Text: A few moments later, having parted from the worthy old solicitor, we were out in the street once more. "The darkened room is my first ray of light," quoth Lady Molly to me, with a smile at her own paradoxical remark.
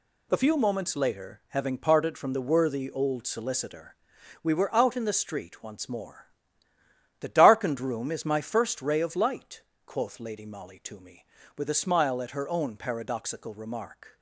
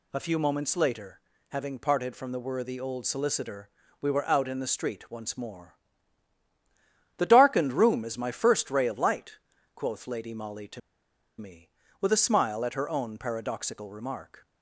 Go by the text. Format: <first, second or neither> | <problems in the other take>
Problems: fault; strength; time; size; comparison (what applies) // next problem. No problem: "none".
first | pauses between "to" and "me"; noticeable; at 10.7 s; 0.58 s long